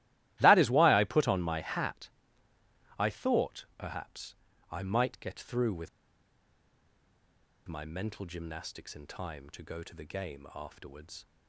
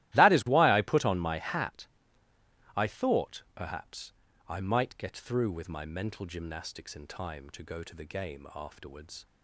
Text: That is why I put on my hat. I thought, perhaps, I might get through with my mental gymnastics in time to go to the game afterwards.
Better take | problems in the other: second | starts louder than the rest; strong; until 1.4 s; 15.5 dB; strong in the second // pauses between "with" and "my"; strong; at 5.8 s; 1.7 s long

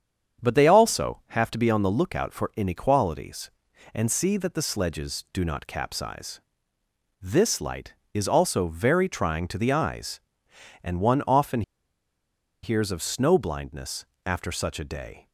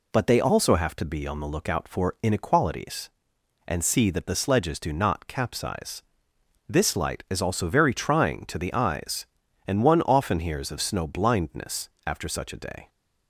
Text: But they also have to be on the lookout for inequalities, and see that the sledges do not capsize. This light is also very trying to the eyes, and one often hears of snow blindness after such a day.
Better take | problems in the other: second | starts louder than the rest; strong; until 1.5 s; 7.5 dB // pauses between "often" and "hears"; at 11.6 s; 1.0 s long // pauses between "blindness" and "after"; slight; at 14.0 s; 0.22 s long; slight in the second

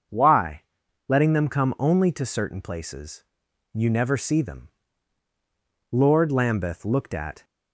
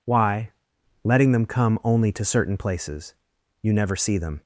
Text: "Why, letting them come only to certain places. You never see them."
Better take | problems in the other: second | starts louder than the rest; until 1.5 s; 6.5 dB // goes on to say "Lord Lambeth looked at"; from 5.9 s on; 1.5 s long

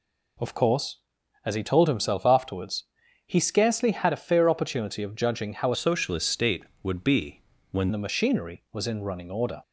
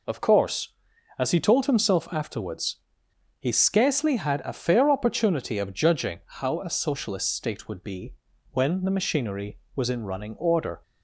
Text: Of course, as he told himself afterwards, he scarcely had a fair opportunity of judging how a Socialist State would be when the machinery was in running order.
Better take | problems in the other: second | changes voice from "Socialist" to "when"; from 5.7 to 7.8 s; 2.1 s long // pauses between "be" and "when"; slight; at 7.3 s; 0.32 s long; slight in the second

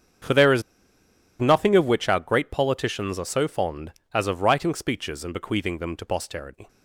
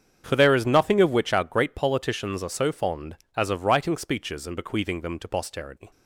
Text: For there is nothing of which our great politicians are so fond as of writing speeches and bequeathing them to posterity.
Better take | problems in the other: second | starts louder than the rest; strong; until 2.0 s; 8 dB; strong in the second // pauses between "is" and "nothing"; noticeable; at 0.6 s; 0.77 s long

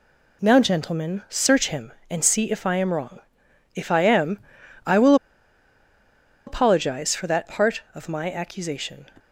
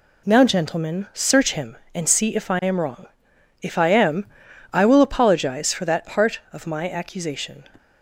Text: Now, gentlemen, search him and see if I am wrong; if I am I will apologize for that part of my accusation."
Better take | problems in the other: second | pauses between "am" and "I"; noticeable; at 4.3 s; 0.48 s long; noticeable in the second // pauses between "will" and "apologize"; strong; at 5.1 s; 1.3 s long

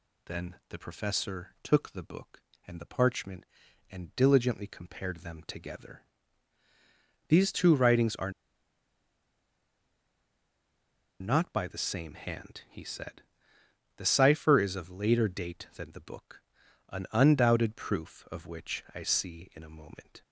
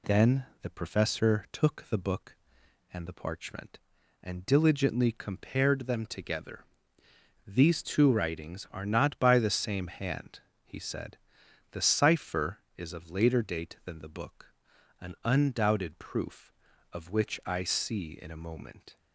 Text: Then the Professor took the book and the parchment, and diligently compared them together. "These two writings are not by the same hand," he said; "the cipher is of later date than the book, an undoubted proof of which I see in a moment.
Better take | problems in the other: second | pauses between "Then" and "the"; slight; at 0.5 s; 0.16 s long; slight in the second // pauses between "are" and "not"; strong; at 8.3 s; 2.9 s long

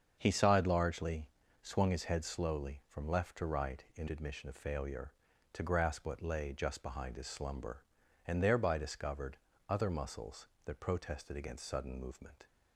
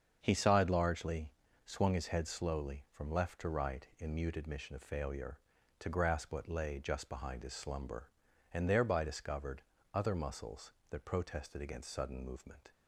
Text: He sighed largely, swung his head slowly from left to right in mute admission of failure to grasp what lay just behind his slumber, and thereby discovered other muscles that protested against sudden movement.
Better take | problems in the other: second | starts louder than the rest; until 1.1 s; 7 dB; strong in the second // skips "mute"; at 4.0 s // pauses between "discovered" and "other"; slight; at 9.3 s; 0.32 s long; slight in the second

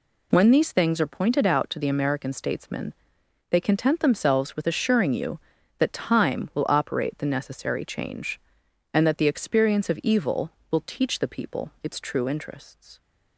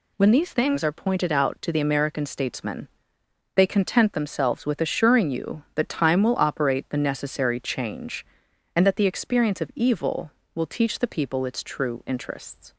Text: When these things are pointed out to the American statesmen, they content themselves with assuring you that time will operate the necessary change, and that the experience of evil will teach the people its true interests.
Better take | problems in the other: neither | none

